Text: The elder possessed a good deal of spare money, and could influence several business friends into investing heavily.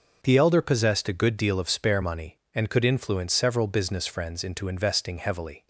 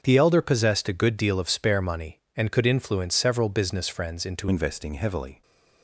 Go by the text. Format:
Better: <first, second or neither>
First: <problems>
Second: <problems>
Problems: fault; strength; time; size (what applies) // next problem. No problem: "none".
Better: first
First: none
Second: starts louder than the rest; until 1.0 s; 7 dB // changes voice at "investing"; from 4.4 s on; 1.0 s long